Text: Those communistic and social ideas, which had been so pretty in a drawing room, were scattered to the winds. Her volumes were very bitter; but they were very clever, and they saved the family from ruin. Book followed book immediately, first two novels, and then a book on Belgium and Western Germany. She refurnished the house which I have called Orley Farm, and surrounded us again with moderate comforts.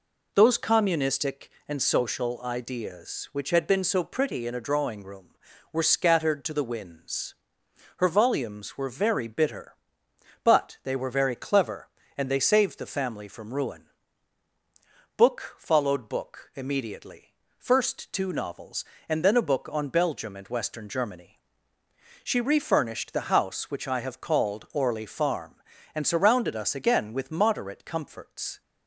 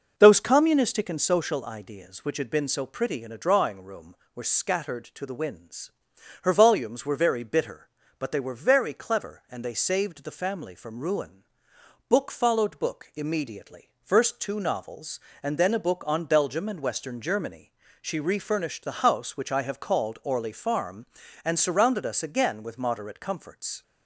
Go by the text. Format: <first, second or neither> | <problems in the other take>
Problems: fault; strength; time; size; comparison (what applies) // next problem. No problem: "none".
first | starts louder than the rest; noticeable; until 1.1 s; 5.5 dB